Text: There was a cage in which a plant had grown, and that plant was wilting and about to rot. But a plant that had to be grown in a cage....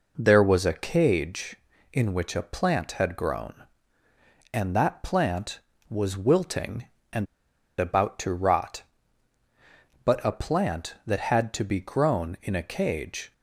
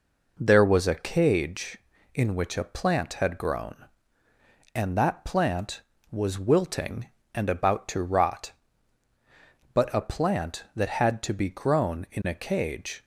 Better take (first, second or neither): second